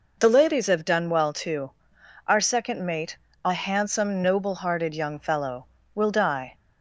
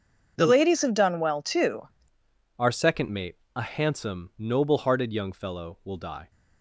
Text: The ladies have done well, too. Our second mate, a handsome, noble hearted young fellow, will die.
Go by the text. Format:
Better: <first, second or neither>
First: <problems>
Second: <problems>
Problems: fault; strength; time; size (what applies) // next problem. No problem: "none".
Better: first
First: none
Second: changes voice at "Our"; from 2.5 s on; 3.8 s long